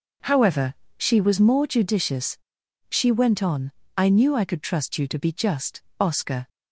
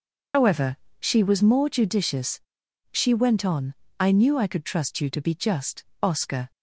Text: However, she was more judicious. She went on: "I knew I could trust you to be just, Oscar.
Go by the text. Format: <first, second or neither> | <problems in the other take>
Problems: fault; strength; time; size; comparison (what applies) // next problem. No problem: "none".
first | loses the start of "However"; at 0.3 s; 100 ms